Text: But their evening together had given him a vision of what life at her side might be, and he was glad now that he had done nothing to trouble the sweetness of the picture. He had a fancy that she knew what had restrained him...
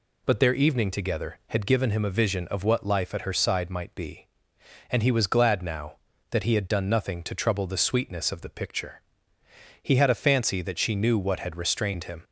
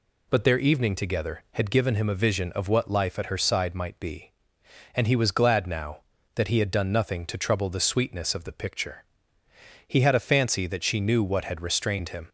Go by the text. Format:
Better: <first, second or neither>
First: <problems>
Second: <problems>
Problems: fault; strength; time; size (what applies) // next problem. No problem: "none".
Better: neither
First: none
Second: none